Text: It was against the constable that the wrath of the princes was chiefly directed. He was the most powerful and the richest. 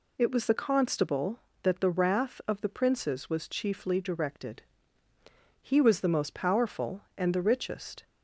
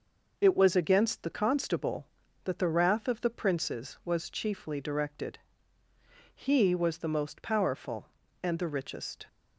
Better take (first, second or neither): second